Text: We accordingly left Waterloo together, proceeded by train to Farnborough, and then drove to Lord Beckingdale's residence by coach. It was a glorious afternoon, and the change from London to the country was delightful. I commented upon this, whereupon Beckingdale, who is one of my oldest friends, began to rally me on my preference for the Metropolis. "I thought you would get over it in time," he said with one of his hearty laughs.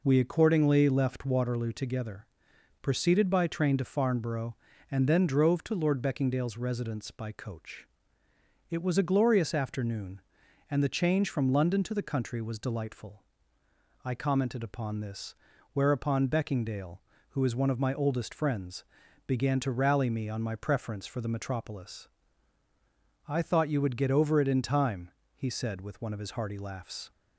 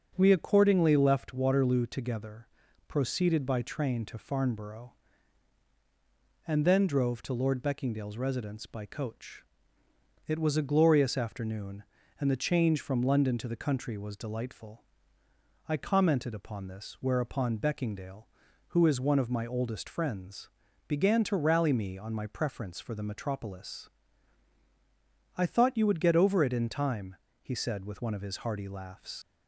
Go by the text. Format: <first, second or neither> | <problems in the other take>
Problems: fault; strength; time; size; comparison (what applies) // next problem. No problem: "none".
first | starts louder than the rest; until 1.1 s; 6.5 dB // leaves "laughs" unfinished; at 29.2 s; 80 ms